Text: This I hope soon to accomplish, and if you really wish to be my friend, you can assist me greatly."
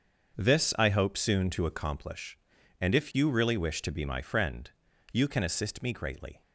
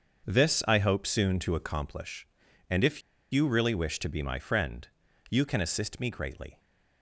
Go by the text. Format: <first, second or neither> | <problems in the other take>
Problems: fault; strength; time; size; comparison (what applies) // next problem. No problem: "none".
first | starts louder than the rest; until 1.3 s; 6.5 dB; also in the first // pauses between "if" and "you"; slight; at 3.0 s; 0.32 s long